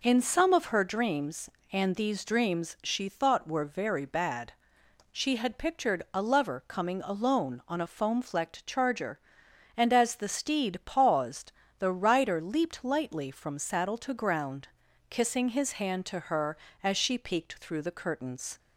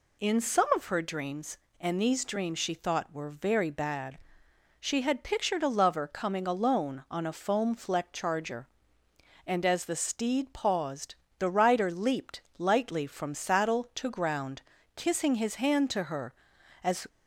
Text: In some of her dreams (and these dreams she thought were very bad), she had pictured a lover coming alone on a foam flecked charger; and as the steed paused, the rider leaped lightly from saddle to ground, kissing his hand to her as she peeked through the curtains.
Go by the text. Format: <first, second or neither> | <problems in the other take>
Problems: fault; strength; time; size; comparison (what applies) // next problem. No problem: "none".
first | pauses between "leaped" and "lightly"; slight; at 12.4 s; 0.16 s long // stops before "she peeked through the curtains"; at 17.0 s